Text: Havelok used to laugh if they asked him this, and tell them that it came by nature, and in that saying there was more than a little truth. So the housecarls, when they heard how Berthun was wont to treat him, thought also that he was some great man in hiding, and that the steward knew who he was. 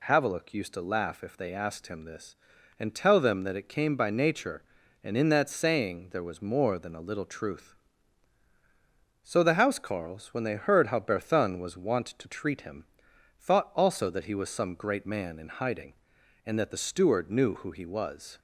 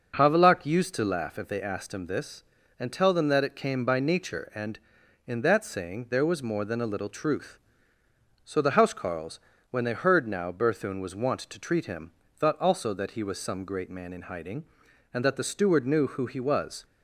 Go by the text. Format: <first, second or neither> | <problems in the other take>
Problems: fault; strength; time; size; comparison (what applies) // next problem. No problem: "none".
first | says "now" for "how"; at 10.2 s